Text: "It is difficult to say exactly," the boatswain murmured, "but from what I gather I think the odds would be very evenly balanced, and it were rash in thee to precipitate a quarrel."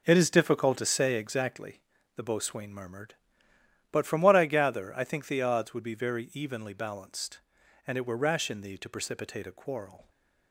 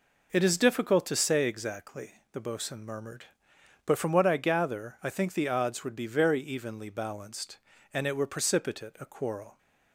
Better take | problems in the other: first | skips "rash in thee to"; at 8.2 s

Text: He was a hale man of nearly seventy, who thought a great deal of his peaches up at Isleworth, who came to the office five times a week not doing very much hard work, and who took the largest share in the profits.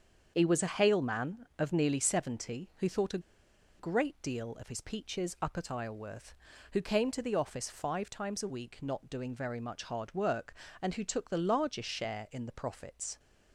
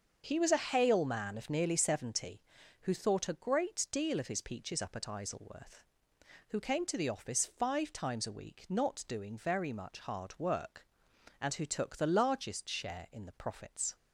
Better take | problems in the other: second | starts louder than the rest; until 1.3 s; 7 dB; also in the second // pauses between "a" and "great"; noticeable; at 3.1 s; 0.59 s long

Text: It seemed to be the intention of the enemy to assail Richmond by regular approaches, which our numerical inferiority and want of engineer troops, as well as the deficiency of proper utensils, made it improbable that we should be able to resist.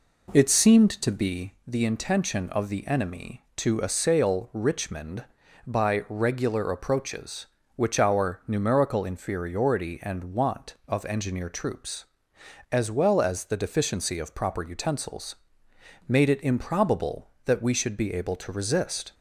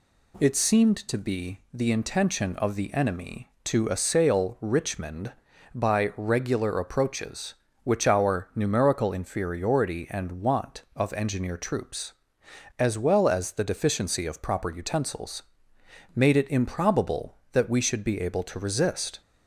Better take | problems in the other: second | starts louder than the rest; until 1.5 s; 3.5 dB

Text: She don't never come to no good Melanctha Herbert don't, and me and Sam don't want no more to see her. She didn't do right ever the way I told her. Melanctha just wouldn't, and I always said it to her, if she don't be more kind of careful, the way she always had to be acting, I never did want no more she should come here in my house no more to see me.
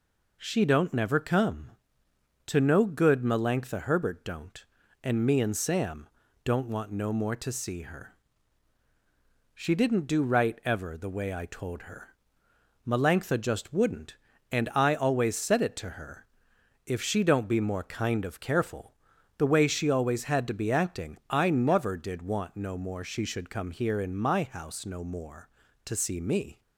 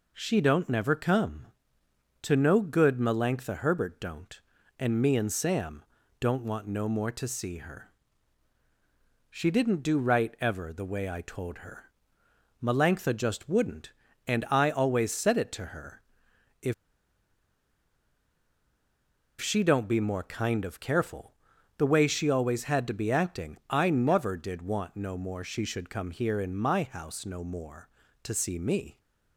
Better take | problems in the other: first | pauses between "Sam" and "don't"; at 5.8 s; 0.38 s long; also in the first // pauses between "if" and "she"; strong; at 16.7 s; 2.6 s long

